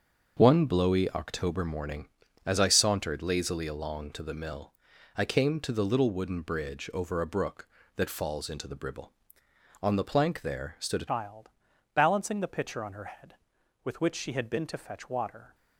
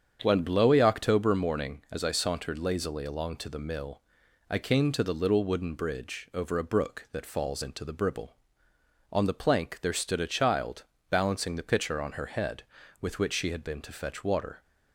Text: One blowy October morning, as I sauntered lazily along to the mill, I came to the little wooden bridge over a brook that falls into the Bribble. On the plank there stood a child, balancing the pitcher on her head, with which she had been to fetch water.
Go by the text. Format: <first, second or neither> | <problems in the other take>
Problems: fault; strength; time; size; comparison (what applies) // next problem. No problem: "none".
second | starts louder than the rest; until 1.3 s; 6 dB; strong in the second // changes voice at "child"; from 11.0 s on; 4.5 s long